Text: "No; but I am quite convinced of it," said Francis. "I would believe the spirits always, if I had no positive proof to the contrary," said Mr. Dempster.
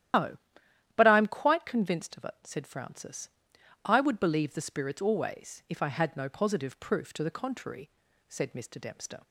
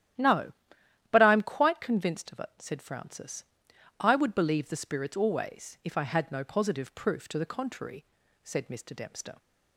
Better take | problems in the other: second | loses the start of "No"; at 0.1 s; 115 ms // starts louder than the rest; strong; until 1.7 s; 12 dB; strong in the second

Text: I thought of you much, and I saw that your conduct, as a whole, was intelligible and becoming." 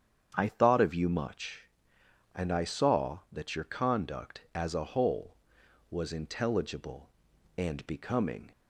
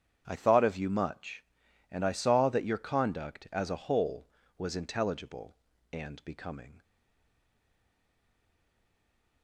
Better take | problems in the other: first | starts louder than the rest; strong; until 1.2 s; 8.5 dB; strong in the first // stays silent after the last word; strong; from 6.8 s on; 2.6 s long

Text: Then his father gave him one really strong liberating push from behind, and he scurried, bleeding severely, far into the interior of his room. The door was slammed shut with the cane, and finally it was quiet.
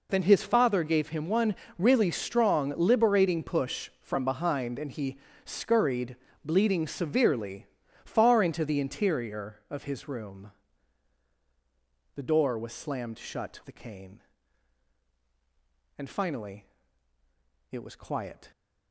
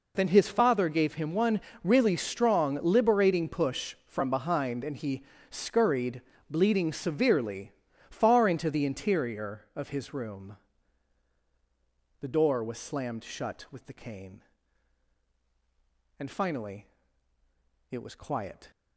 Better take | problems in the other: second | pauses between "one" and "really"; slight; at 1.5 s; 0.24 s long; slight in the second // pauses between "he" and "scurried"; slight; at 5.1 s; 0.28 s long; slight in the second // skips "with"; at 13.6 s // pauses between "finally" and "it"; at 16.6 s; 1.0 s long; also in the second

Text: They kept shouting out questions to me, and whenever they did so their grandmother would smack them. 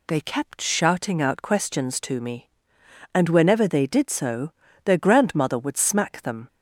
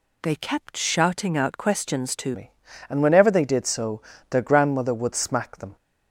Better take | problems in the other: first | changes voice at "me"; from 2.3 s on; 3.4 s long // pauses between "so" and "their"; slight; at 3.9 s; 0.30 s long; slight in the first

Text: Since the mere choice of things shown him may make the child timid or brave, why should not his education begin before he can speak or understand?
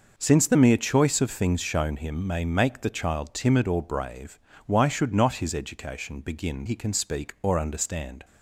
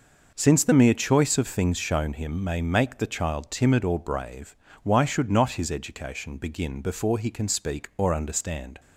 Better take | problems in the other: second | skips "before"; at 6.6 s

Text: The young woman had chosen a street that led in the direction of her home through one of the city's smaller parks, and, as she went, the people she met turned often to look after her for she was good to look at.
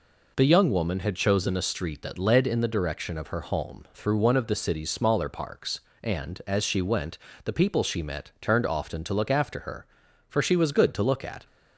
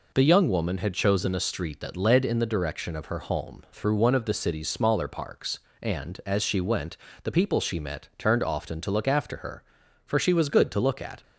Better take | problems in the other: neither | none

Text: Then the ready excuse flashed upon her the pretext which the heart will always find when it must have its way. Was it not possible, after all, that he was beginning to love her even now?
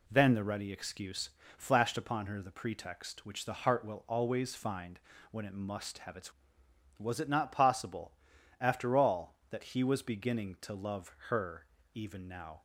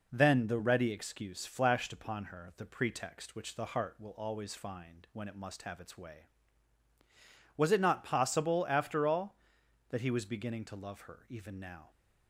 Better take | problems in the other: second | pauses between "excuse" and "flashed"; slight; at 1.2 s; 0.28 s long // pauses between "find" and "when"; slight; at 4.9 s; 0.32 s long // skips "way"; at 6.6 s // pauses between "her" and "even"; slight; at 11.6 s; 0.28 s long

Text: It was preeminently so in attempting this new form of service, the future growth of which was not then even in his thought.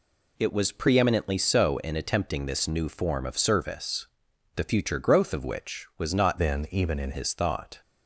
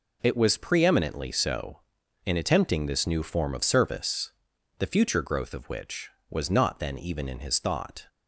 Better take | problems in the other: second | changes voice from "then" to "in"; from 6.3 to 7.1 s; 0.8 s long

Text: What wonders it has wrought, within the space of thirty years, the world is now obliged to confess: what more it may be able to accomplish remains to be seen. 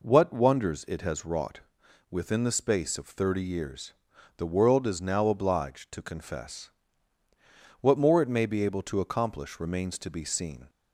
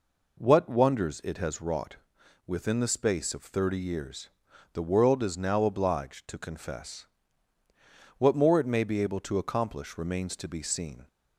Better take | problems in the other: neither | none

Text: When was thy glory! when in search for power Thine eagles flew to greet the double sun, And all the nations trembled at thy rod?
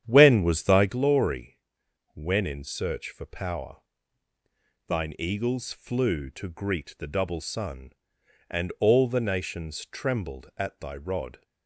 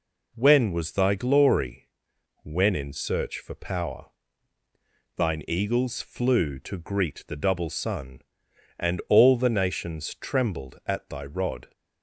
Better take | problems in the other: second | starts louder than the rest; strong; until 0.9 s; 9.5 dB // pauses between "power" and "Thine"; at 3.7 s; 1.1 s long; also in the second

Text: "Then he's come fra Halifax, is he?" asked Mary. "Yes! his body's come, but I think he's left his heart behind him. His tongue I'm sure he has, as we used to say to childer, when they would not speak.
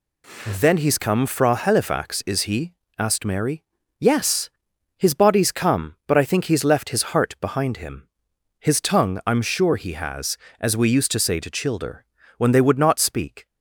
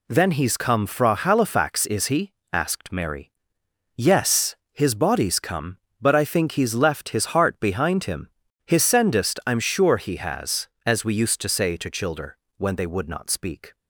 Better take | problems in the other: first | says "sendest" for "tongue"; at 8.8 s

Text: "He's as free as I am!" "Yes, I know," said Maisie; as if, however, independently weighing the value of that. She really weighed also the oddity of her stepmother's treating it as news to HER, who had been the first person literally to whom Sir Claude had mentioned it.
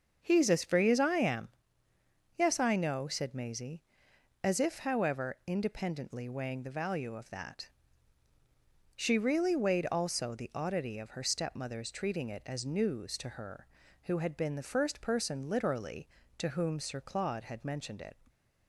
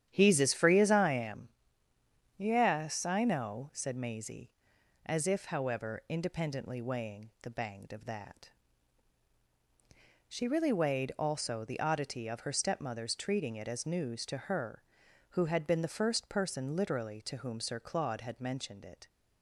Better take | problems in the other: first | starts louder than the rest; strong; until 1.1 s; 10 dB; also in the first // says "banged" for "value"; at 7.4 s

